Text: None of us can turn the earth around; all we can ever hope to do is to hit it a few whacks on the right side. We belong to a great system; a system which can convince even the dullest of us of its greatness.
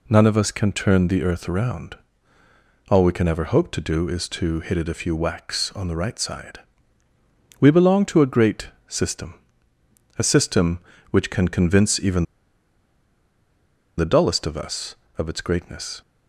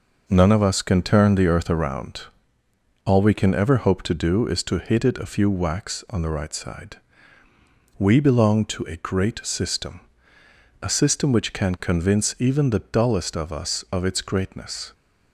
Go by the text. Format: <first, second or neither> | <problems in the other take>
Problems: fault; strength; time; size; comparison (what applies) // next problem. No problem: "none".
second | pauses between "great" and "system"; slight; at 8.6 s; 0.18 s long // pauses between "even" and "the"; strong; at 12.2 s; 1.7 s long